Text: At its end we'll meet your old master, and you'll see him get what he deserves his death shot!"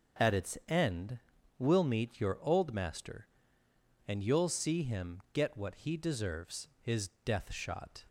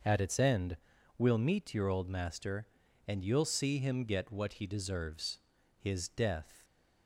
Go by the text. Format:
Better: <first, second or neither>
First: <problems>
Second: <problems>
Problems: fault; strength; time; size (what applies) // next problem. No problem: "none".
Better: first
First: pauses between "end" and "we'll"; at 1.1 s; 0.40 s long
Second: starts louder than the rest; noticeable; until 1.4 s; 6 dB // pauses between "end" and "we'll"; at 0.7 s; 0.42 s long // pauses between "deserves" and "his"; at 5.3 s; 0.42 s long // stops before "shot"; at 6.6 s